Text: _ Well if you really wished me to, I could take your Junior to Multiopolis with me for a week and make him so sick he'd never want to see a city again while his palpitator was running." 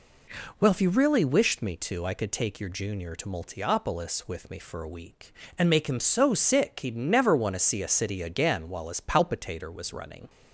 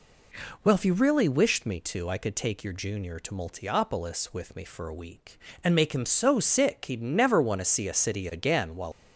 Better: first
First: none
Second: stops before "his palpitator was running"; at 8.9 s

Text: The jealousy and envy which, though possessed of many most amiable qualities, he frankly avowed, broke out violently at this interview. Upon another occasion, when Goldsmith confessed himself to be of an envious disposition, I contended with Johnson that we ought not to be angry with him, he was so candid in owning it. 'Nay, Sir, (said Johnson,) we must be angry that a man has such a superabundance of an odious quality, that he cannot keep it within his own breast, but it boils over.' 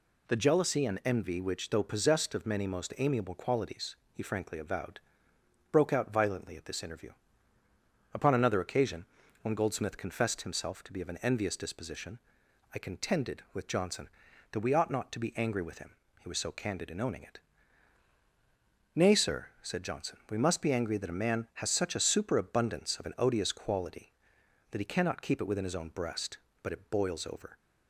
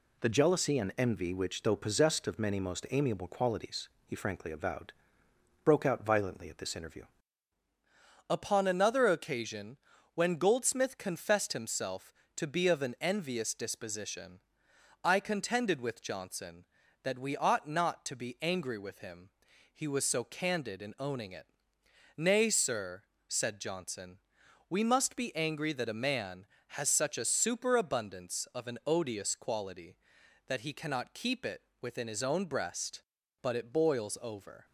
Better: first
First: none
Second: changes voice at "Upon"; from 8.2 s on; 26.4 s long // pauses between "it" and "within"; slight; at 31.6 s; 0.20 s long

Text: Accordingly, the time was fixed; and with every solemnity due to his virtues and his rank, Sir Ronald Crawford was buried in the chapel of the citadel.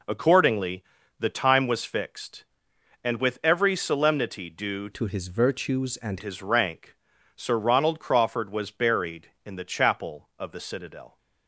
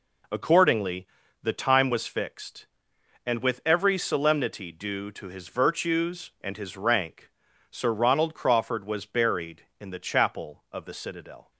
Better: second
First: changes voice from "to" to "and"; from 4.9 to 6.2 s; 1.3 s long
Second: none

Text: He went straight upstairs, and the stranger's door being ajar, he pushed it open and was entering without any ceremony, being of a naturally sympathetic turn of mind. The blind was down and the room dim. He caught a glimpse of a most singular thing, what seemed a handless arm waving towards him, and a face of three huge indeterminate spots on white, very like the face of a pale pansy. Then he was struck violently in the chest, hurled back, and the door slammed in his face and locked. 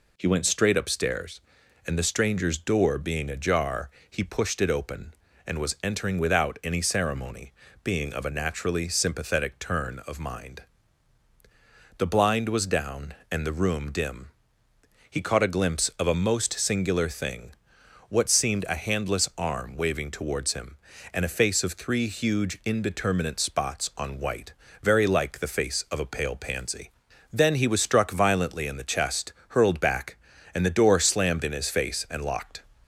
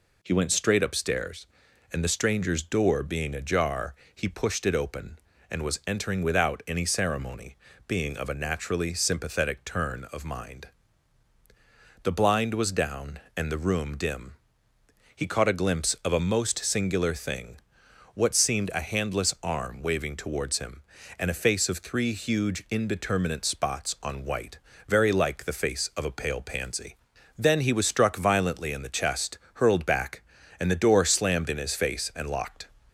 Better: neither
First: none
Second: none

